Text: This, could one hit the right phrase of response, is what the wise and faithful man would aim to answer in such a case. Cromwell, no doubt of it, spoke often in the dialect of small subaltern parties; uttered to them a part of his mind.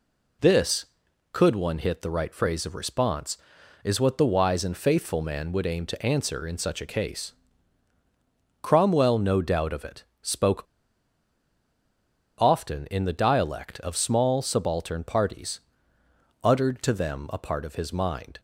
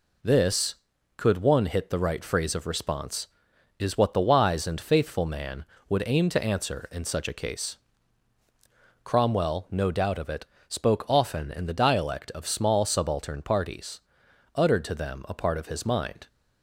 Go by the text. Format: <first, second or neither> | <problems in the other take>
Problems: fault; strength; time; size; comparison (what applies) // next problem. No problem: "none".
second | pauses between "spoke" and "often"; strong; at 10.6 s; 1.7 s long